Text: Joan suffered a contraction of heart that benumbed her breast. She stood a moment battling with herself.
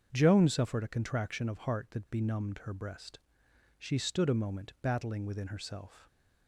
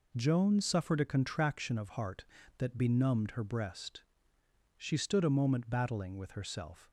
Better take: second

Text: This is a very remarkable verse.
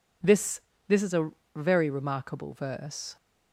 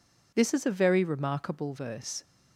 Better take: second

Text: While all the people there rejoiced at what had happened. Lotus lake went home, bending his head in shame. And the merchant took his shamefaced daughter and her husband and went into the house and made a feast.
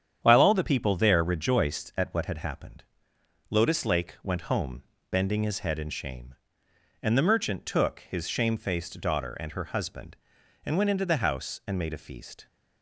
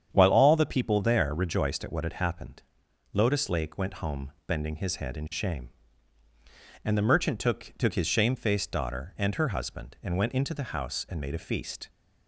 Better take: first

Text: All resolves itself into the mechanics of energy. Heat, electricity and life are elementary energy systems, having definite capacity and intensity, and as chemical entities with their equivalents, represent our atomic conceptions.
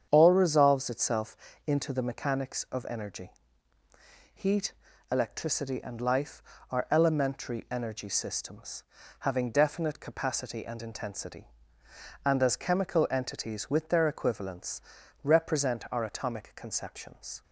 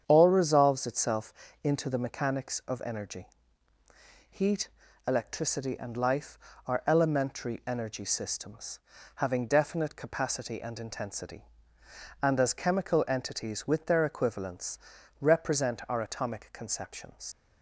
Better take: first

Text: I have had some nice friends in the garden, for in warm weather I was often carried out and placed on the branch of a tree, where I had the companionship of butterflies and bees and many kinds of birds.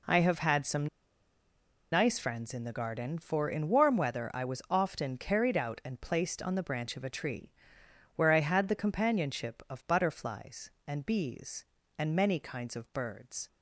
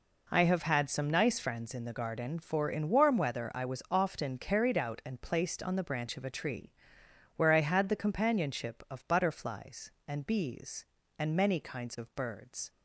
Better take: second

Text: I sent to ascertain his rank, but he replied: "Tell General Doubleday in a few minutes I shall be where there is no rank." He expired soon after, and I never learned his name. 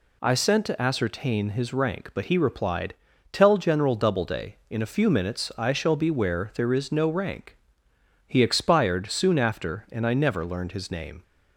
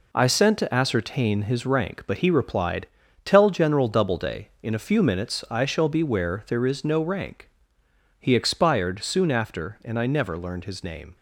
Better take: first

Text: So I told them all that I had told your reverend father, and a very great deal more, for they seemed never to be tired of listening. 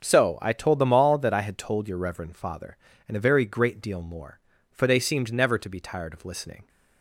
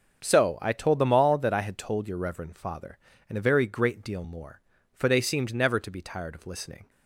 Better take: neither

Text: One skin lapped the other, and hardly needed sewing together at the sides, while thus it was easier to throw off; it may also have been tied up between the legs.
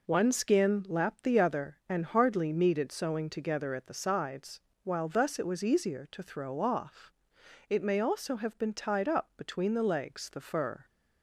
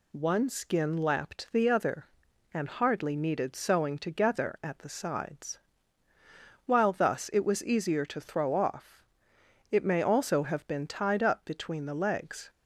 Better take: second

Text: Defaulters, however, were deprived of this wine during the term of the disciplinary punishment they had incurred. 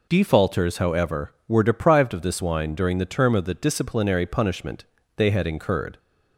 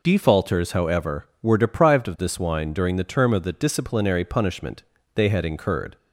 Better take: neither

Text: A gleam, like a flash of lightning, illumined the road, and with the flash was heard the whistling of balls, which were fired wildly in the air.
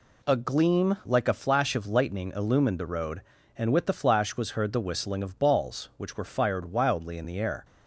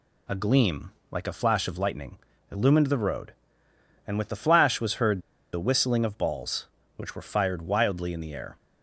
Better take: first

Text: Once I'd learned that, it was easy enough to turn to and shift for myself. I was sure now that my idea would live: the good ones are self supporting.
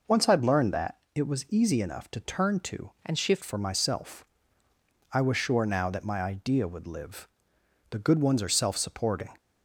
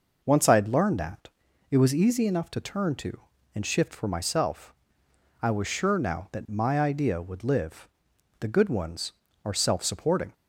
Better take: second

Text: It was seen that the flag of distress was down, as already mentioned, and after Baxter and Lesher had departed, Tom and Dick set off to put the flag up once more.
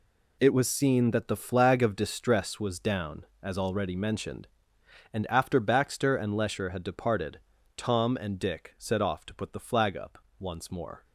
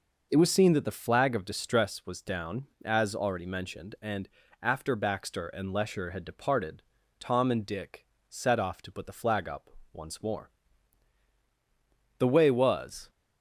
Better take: first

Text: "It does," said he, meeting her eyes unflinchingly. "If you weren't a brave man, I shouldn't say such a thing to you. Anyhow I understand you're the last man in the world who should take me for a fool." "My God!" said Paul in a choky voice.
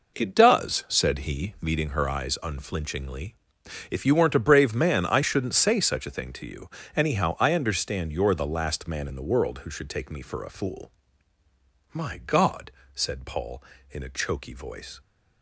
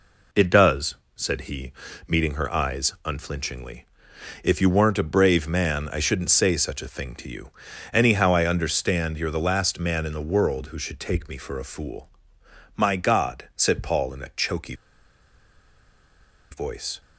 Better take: first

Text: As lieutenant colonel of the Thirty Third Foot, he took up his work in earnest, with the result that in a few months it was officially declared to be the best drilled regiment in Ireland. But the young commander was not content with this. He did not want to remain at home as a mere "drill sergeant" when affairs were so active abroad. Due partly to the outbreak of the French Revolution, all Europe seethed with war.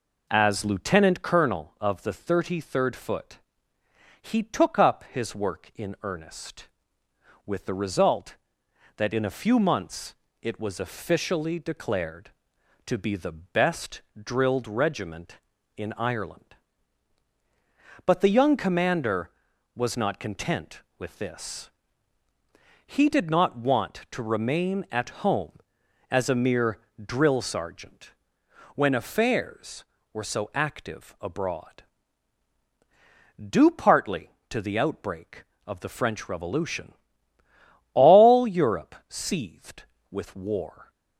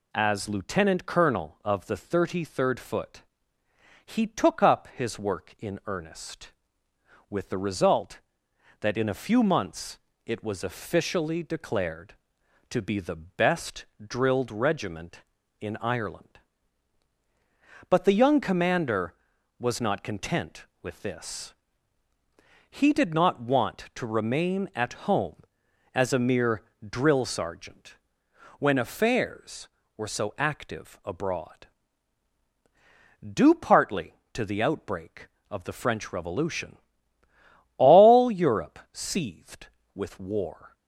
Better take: second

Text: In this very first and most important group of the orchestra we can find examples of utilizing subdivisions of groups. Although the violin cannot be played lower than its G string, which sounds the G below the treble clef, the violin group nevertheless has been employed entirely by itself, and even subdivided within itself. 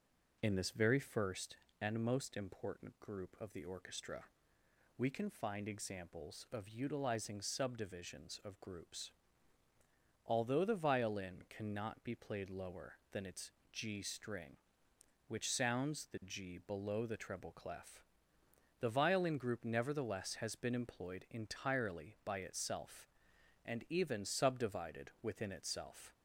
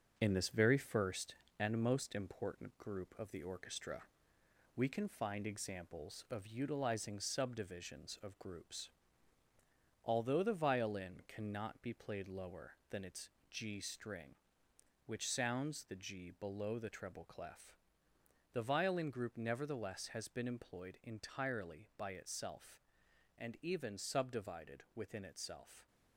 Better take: first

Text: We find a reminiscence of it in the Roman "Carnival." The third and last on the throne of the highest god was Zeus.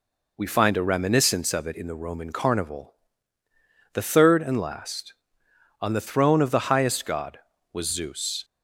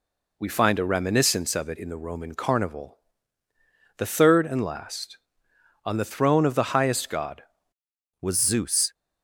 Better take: first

